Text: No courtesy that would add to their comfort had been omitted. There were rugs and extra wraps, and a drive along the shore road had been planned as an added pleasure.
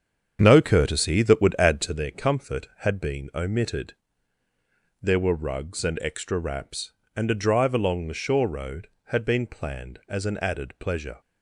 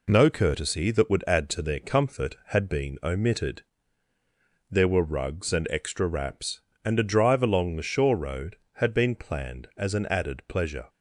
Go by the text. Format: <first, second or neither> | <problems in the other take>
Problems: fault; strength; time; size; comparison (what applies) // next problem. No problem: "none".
second | starts louder than the rest; strong; until 2.0 s; 8 dB